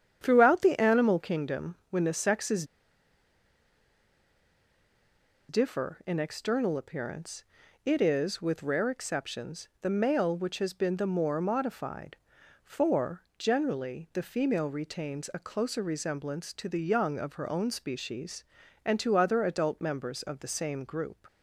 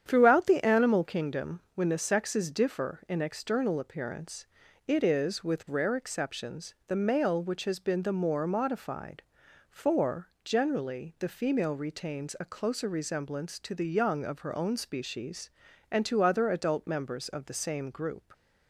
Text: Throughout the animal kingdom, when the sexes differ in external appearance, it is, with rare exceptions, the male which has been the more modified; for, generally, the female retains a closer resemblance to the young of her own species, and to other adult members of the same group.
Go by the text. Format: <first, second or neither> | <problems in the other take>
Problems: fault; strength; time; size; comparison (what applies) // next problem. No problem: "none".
second | starts louder than the rest; strong; until 1.2 s; 9 dB; strong in the second // pauses between "sexes" and "differ"; strong; at 2.6 s; 2.8 s long